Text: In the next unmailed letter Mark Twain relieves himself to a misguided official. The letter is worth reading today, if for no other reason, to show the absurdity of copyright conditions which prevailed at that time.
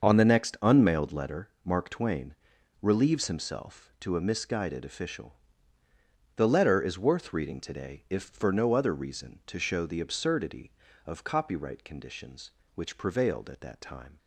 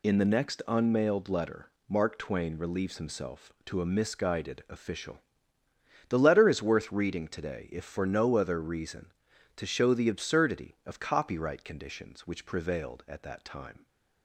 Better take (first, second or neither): second